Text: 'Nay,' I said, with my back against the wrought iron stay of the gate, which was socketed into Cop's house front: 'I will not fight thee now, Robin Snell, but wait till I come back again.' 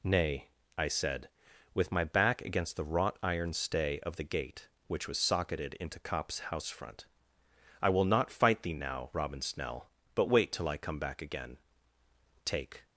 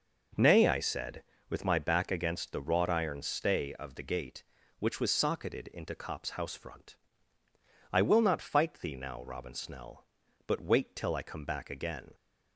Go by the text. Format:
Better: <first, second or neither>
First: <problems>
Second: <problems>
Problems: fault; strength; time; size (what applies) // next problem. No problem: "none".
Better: second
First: goes on to say "Take"; slight; from 12.4 s on; 0.40 s long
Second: none